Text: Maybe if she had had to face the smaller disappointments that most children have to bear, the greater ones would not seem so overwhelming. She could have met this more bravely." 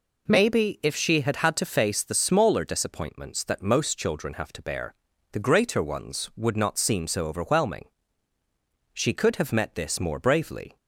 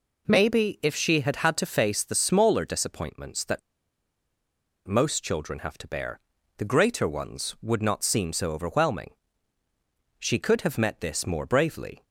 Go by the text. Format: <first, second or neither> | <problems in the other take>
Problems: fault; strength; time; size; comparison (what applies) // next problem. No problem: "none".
first | pauses between "that" and "most"; strong; at 3.6 s; 1.2 s long